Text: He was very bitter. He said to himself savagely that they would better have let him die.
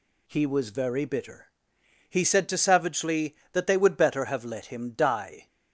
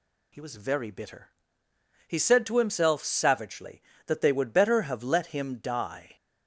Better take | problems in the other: second | skips "himself"; at 2.5 s

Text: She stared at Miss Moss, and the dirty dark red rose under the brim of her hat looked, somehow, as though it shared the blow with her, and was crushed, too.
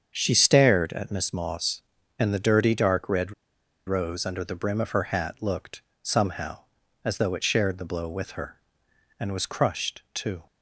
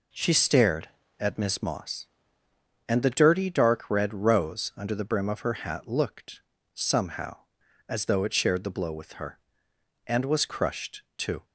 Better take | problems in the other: second | starts louder than the rest; strong; until 1.1 s; 7.5 dB // pauses between "red" and "rose"; noticeable; at 3.3 s; 0.55 s long

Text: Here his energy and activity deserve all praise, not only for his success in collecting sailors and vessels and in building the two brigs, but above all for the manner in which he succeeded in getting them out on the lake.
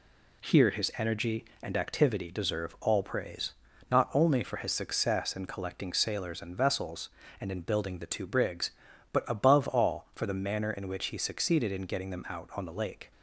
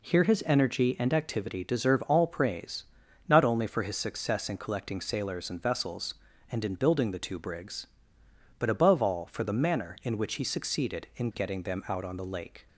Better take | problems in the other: neither | none

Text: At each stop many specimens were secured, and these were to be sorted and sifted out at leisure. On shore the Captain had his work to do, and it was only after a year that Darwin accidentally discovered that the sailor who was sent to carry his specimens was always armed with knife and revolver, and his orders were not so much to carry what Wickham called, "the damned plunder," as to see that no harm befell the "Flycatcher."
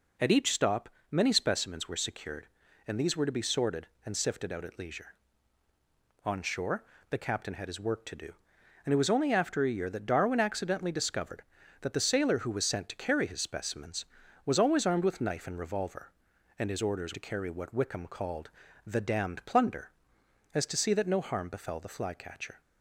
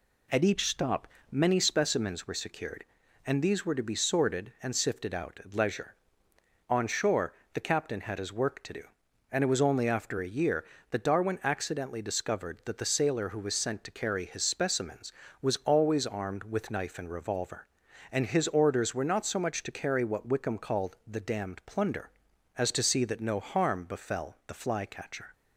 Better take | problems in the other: second | pauses between "stop" and "many"; slight; at 0.8 s; 0.22 s long; slight in the second // pauses between "shore" and "the"; slight; at 6.8 s; 0.28 s long; slight in the second // skips "were not so much"; at 17.1 s

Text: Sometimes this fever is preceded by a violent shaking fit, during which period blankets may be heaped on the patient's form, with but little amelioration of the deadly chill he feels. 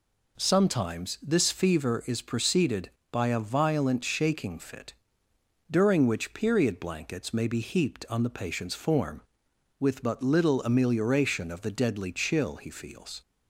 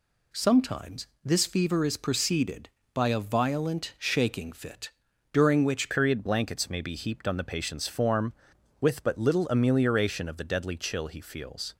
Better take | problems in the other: first | pauses between "Sometimes" and "this"; slight; at 1.0 s; 0.16 s long // changes voice at "period"; from 5.8 s on; 5.9 s long

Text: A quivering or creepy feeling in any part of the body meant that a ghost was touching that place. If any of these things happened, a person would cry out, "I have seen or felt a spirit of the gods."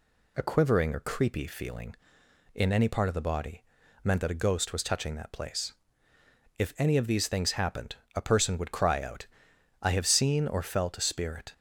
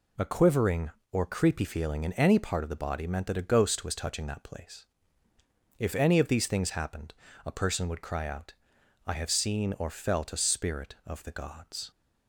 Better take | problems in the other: second | pauses between "body" and "meant"; at 3.6 s; 0.40 s long // stops before "of the gods"; at 11.5 s

